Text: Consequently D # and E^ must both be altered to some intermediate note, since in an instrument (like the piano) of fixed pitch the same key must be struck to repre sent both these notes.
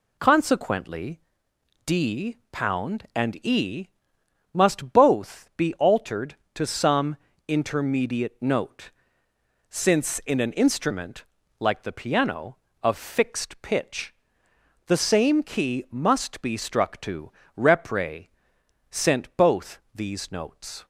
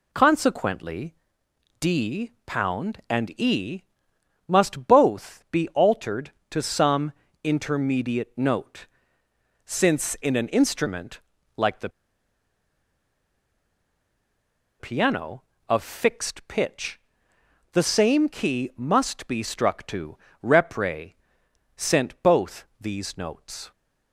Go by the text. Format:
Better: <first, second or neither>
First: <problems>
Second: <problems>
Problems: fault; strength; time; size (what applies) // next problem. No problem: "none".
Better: first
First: pauses between "Consequently" and "D"; noticeable; at 1.2 s; 0.66 s long // pauses between "E" and "must"; noticeable; at 3.8 s; 0.64 s long // pauses between "some" and "intermediate"; slight; at 7.1 s; 0.30 s long // pauses between "pitch" and "the"; noticeable; at 14.1 s; 0.74 s long // pauses between "to" and "repre"; slight; at 17.3 s; 0.26 s long // pauses between "repre" and "sent"; noticeable; at 18.2 s; 0.62 s long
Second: pauses between "Consequently" and "D"; noticeable; at 1.1 s; 0.66 s long // pauses between "E" and "must"; noticeable; at 3.8 s; 0.64 s long // pauses between "some" and "intermediate"; slight; at 7.1 s; 0.30 s long // pauses between "the" and "piano"; strong; at 11.8 s; 2.9 s long // pauses between "pitch" and "the"; noticeable; at 16.9 s; 0.74 s long // pauses between "to" and "repre"; slight; at 20.1 s; 0.26 s long // pauses between "repre" and "sent"; noticeable; at 21.1 s; 0.62 s long